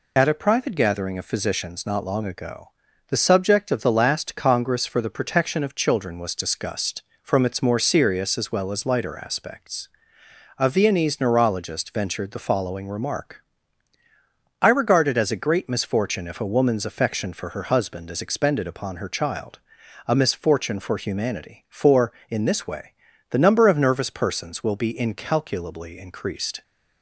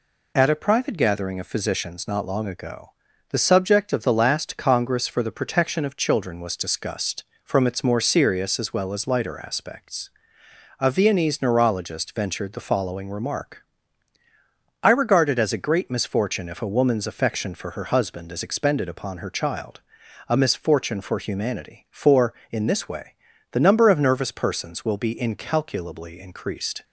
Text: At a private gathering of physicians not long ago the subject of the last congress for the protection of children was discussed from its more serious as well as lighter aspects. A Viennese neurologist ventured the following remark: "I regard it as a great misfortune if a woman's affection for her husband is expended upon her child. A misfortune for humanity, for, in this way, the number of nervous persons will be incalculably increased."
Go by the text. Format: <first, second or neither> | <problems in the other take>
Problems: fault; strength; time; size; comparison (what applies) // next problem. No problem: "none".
second | loses the start of "At"; at 0.1 s; 25 ms // pauses between "ago" and "the"; at 2.6 s; 0.38 s long; also in the second